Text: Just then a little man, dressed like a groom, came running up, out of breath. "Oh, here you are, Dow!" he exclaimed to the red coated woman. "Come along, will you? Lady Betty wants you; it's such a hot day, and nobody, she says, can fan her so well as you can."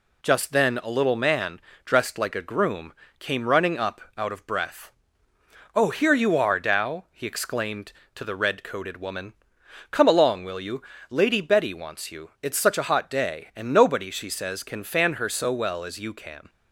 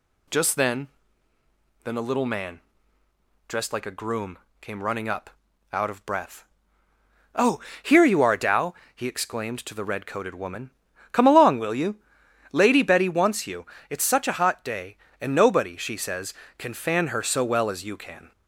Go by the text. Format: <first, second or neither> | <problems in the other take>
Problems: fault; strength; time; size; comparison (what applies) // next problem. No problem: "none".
first | says "then" twice; at 1.8 s